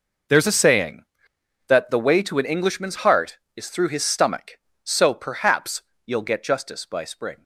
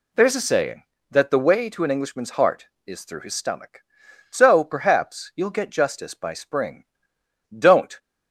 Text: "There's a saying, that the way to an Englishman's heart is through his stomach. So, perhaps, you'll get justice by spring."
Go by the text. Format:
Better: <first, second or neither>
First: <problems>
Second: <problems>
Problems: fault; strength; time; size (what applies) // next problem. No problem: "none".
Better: first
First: none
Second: goes on to say "Don't"; slight; from 7.5 s on; 0.40 s long